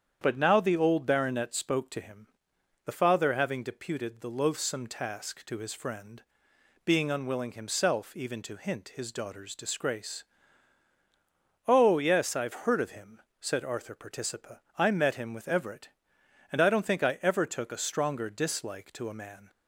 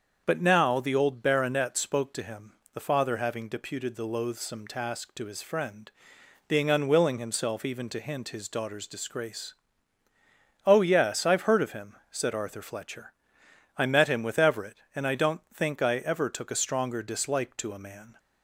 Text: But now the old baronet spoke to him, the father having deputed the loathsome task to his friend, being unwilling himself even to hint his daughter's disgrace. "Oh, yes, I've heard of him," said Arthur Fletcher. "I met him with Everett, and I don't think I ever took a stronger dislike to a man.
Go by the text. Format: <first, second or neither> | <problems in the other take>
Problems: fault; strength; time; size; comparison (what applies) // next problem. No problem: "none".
second | starts louder than the rest; strong; until 1.2 s; 8.5 dB; also in the second // says "Participa" for "Fletcher"; at 13.9 s